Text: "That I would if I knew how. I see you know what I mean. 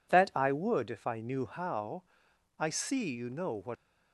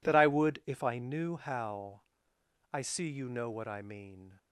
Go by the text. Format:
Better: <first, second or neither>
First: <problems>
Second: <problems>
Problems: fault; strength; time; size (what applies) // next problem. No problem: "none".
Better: second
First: stops before "I mean"; at 3.7 s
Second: none